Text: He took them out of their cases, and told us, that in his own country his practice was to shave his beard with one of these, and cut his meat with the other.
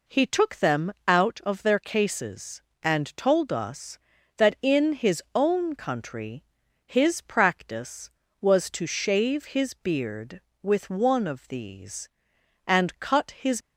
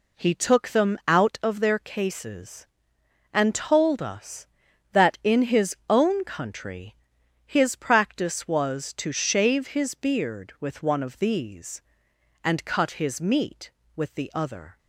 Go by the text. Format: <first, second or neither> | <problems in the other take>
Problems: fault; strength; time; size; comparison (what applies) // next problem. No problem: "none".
second | pauses between "them" and "out"; slight; at 0.9 s; 0.16 s long // pauses between "country" and "his"; at 6.4 s; 0.40 s long; noticeable in the second // stops before "meat with the other"; at 13.6 s